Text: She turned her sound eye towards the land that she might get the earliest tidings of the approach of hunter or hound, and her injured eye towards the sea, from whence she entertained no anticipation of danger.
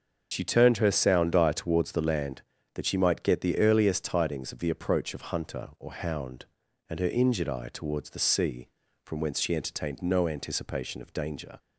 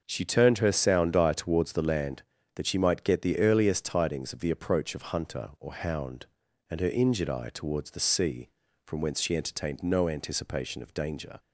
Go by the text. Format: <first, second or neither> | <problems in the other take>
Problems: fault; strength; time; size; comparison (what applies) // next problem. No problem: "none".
second | loses the start of "She"; at 0.3 s; 70 ms // starts louder than the rest; until 1.3 s; 6.5 dB; also in the second